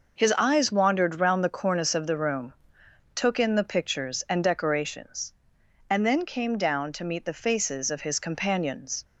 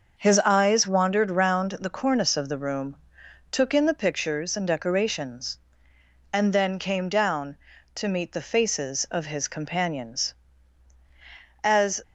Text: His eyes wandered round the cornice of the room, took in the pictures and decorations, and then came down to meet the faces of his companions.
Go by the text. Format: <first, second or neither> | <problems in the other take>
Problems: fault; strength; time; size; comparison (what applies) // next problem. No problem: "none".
first | starts louder than the rest; noticeable; until 1.2 s; 6 dB // goes on to say "As"; slight; from 11.6 s on; 0.40 s long